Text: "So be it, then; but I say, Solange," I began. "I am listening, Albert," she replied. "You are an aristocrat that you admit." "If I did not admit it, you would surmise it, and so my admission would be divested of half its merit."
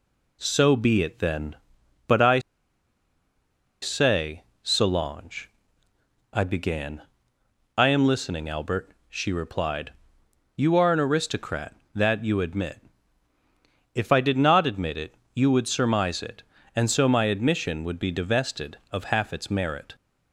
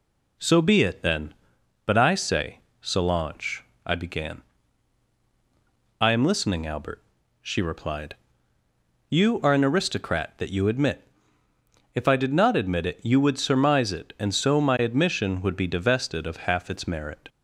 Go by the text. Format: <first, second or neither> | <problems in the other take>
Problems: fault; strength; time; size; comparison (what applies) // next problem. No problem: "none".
second | pauses between "I" and "say"; strong; at 2.3 s; 1.4 s long